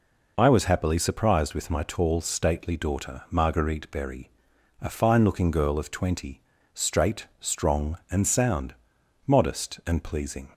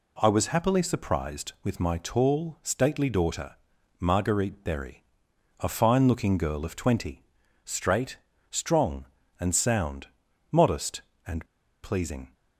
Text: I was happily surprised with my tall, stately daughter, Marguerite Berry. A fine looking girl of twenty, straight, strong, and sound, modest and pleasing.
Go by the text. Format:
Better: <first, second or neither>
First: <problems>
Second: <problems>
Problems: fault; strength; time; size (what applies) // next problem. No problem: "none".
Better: first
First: none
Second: pauses between "and" and "pleasing"; at 11.4 s; 0.37 s long